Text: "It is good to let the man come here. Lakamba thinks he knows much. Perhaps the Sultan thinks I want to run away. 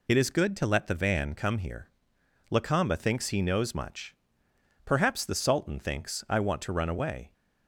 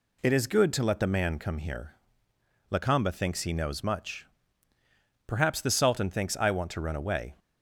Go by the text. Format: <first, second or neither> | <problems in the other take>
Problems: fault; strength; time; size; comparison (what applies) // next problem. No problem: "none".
second | says "van" for "man"; at 0.9 s